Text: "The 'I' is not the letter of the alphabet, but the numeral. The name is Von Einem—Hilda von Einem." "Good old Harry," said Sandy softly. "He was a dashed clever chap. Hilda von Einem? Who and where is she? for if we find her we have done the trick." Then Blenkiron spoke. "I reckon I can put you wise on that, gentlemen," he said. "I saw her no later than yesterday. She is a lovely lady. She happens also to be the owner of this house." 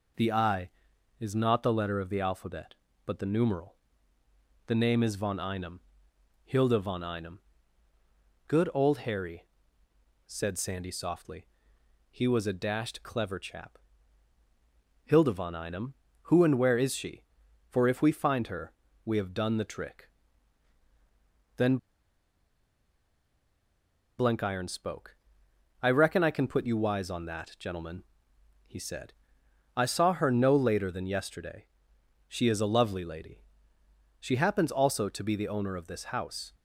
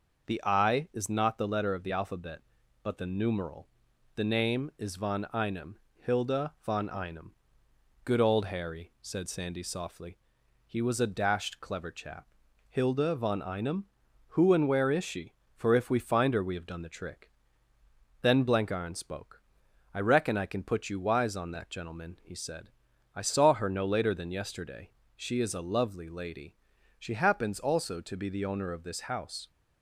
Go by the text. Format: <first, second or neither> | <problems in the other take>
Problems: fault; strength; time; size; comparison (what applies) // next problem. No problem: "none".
second | pauses between "her" and "we"; slight; at 18.7 s; 0.32 s long // pauses between "Then" and "Blenkiron"; strong; at 21.7 s; 2.4 s long